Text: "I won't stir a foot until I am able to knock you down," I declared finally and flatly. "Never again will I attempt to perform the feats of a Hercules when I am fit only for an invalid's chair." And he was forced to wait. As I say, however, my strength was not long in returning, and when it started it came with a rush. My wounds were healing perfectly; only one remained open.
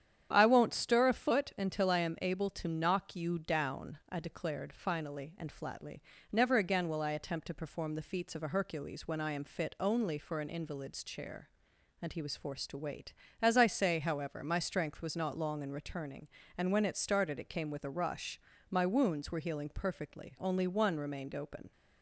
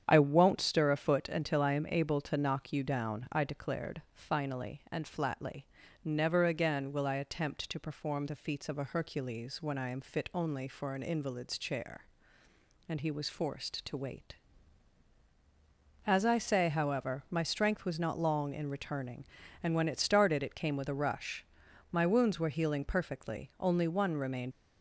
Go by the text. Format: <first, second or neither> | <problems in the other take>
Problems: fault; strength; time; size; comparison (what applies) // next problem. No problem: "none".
first | starts louder than the rest; strong; until 1.0 s; 8.5 dB; strong in the first // stops before "open"; at 24.5 s